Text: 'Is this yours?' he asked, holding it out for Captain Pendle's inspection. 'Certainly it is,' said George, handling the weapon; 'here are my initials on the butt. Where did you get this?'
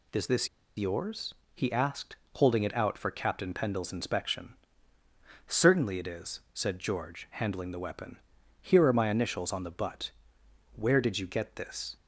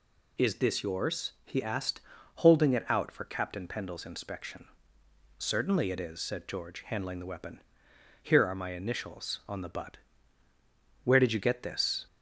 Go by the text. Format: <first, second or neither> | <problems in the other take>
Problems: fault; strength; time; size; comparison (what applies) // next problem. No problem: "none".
second | pauses between "this" and "yours"; slight; at 0.4 s; 0.29 s long